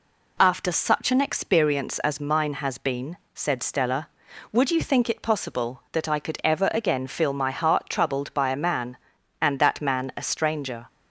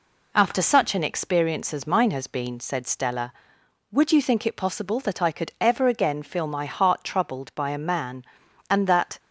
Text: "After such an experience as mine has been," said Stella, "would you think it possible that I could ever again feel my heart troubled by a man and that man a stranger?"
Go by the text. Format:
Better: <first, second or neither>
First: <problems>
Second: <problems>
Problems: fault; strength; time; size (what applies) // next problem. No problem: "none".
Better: first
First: none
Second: stops before "man a stranger"; at 9.1 s